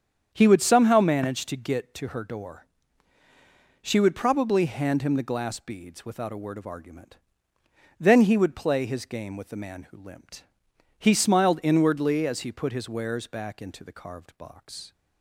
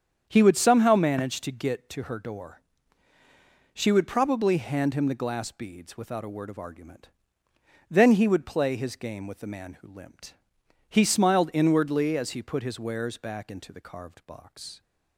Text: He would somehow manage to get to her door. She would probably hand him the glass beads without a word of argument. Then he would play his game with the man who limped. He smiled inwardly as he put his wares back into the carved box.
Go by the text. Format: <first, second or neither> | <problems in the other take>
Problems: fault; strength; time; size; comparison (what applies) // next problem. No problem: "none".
neither | starts louder than the rest; strong; the same in both